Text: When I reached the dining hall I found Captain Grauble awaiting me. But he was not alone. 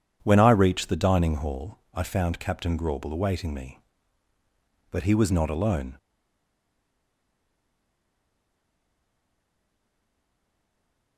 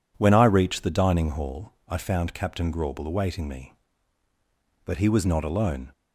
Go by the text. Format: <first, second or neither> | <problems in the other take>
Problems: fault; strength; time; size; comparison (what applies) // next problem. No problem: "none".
second | pauses between "hall" and "I"; slight; at 1.7 s; 0.16 s long; slight in the second // stays silent after the last word; strong; from 5.9 s on; 5.2 s long